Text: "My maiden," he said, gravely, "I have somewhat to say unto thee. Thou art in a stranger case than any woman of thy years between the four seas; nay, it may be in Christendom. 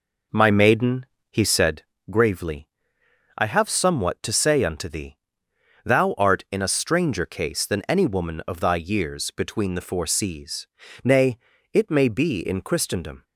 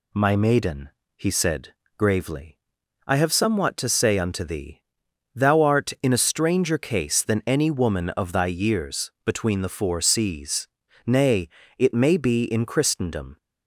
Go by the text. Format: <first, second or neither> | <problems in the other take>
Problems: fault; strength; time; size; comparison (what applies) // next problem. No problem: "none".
second | starts louder than the rest; noticeable; until 1.8 s; 4.5 dB